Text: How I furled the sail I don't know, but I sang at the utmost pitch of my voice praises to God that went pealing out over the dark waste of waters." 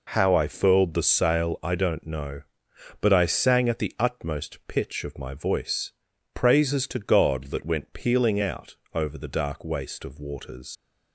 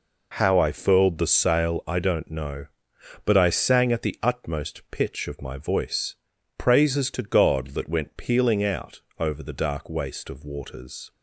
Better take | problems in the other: second | pauses between "voice" and "praises"; at 5.9 s; 0.42 s long; also in the second // pauses between "out" and "over"; slight; at 8.7 s; 0.18 s long; slight in the second // leaves "waters" unfinished; at 10.7 s; 115 ms

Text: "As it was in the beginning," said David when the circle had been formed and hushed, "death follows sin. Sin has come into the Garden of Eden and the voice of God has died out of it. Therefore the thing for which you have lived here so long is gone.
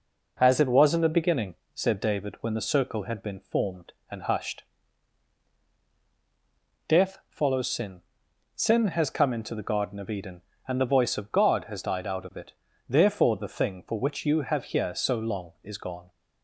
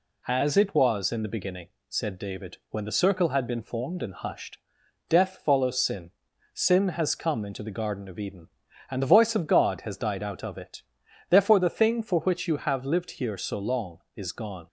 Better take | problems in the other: second | skips "lived"; at 14.6 s

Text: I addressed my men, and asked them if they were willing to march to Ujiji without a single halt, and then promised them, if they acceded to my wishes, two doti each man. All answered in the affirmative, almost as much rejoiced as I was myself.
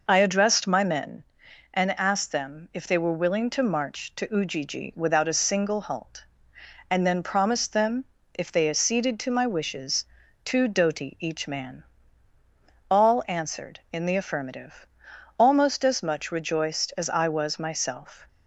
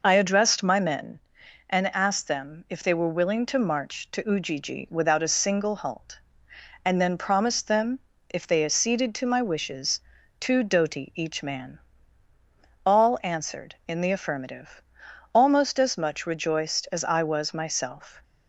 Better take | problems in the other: neither | none

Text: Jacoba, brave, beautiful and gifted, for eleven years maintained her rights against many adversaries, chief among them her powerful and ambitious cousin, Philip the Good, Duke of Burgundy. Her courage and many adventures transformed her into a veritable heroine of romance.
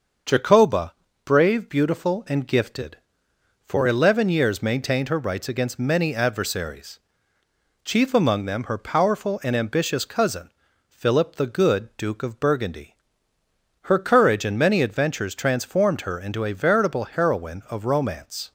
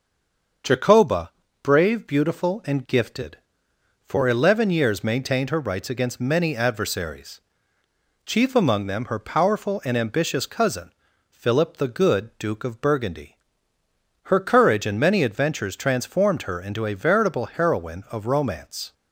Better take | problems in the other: first | stays silent before the first word; slight; until 0.6 s; 0.6 s long // starts louder than the rest; until 2.0 s; 6.5 dB; also in the first

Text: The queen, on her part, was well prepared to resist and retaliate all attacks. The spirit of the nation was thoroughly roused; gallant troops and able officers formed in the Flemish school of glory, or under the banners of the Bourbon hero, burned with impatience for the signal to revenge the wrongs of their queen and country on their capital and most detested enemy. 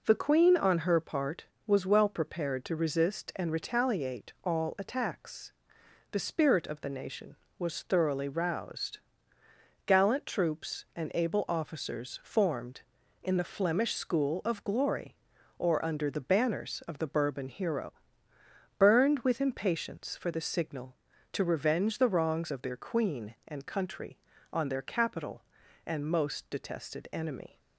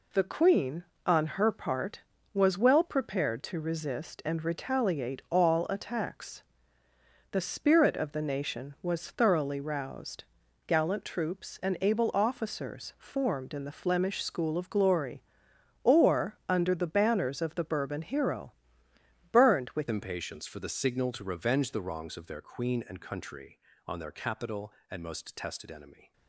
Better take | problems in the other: first | changes voice at "impatience"; from 19.9 s on; 6.2 s long

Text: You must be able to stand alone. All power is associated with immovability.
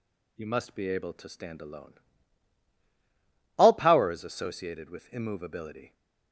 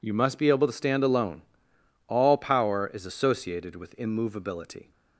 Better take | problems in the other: neither | none

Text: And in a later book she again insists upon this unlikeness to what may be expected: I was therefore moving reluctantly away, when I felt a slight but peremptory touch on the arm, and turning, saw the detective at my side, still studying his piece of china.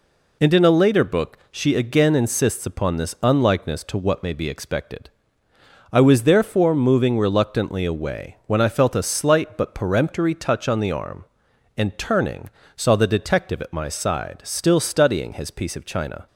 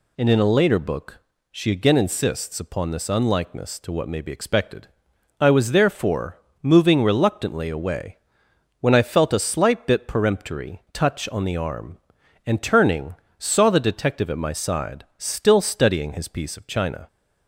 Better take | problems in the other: first | pauses between "book" and "she"; slight; at 1.1 s; 0.36 s long // pauses between "therefore" and "moving"; slight; at 6.3 s; 0.24 s long // says "bit" for "but"; at 9.8 s

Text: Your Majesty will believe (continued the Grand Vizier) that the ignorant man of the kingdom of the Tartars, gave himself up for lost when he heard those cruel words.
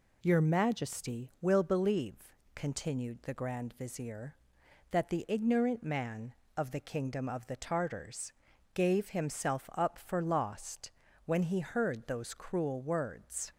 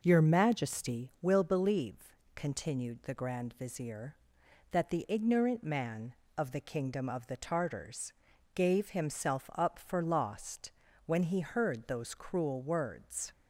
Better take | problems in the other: first | starts louder than the rest; noticeable; until 1.0 s; 5.5 dB // pauses between "lost" and "when"; slight; at 10.7 s; 0.34 s long; slight in the first

